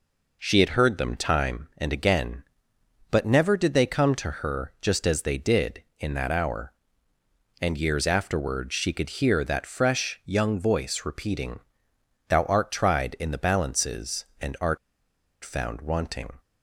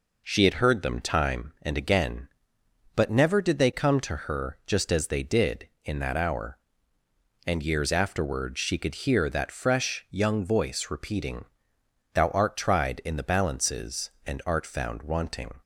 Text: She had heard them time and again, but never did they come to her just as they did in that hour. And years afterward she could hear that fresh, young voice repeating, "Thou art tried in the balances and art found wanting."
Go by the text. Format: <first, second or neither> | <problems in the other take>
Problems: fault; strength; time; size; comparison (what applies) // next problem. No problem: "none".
second | pauses between "art" and "found"; noticeable; at 14.7 s; 0.65 s long